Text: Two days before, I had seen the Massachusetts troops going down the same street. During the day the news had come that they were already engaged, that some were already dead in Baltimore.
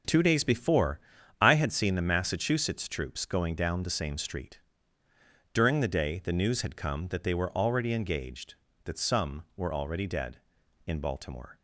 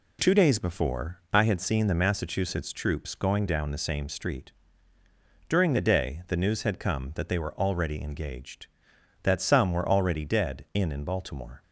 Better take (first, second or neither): first